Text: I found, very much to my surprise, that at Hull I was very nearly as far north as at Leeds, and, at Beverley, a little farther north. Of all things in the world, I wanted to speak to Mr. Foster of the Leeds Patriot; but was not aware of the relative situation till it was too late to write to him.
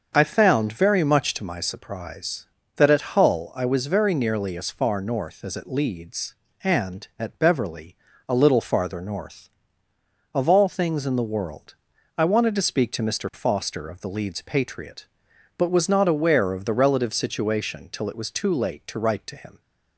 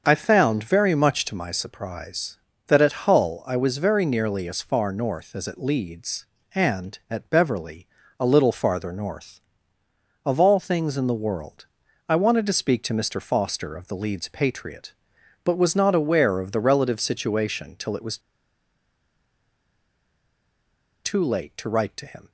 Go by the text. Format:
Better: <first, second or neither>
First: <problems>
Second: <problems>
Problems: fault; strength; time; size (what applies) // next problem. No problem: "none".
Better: first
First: starts louder than the rest; until 1.1 s; 6.5 dB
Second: starts louder than the rest; until 1.0 s; 6.5 dB // pauses between "was" and "too"; strong; at 18.1 s; 2.8 s long